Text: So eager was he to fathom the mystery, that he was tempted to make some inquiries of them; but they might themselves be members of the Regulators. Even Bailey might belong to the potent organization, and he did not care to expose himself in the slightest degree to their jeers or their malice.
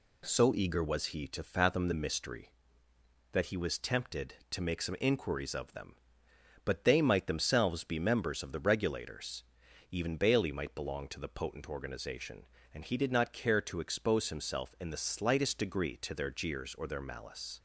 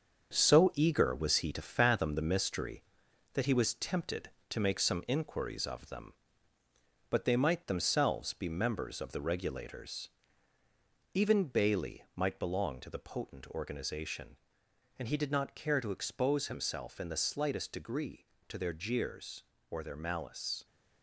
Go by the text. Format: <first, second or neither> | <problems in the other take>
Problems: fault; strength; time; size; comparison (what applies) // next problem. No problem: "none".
first | gets quieter; noticeable; throughout; 6 dB